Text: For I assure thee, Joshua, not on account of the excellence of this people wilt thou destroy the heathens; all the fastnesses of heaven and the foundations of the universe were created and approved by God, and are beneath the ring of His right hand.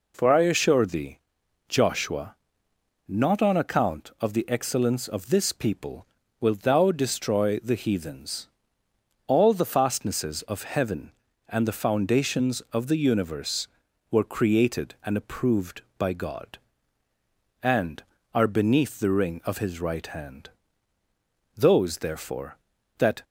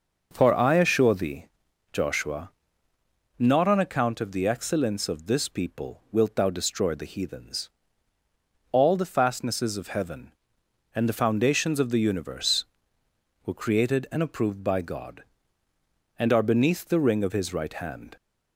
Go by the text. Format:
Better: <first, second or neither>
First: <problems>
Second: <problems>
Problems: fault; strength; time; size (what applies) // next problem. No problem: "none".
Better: second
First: pauses between "people" and "wilt"; slight; at 6.0 s; 0.32 s long // goes on to say "Those therefore that"; from 21.5 s on; 1.6 s long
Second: none